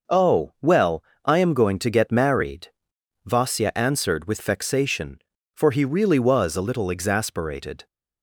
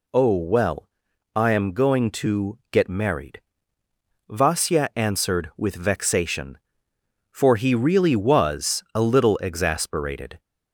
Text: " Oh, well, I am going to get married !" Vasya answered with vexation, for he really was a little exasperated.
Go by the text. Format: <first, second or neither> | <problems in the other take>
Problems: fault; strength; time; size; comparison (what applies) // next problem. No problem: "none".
neither | none